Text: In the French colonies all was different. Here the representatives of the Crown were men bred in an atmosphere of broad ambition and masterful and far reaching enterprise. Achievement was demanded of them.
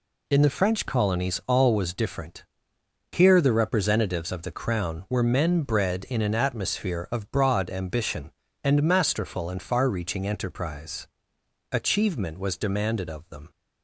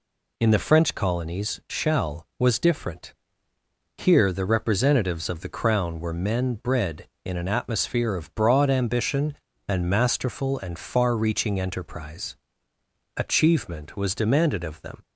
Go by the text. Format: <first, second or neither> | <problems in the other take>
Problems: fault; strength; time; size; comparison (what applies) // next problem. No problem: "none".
first | says "shall" for "all"; at 1.6 s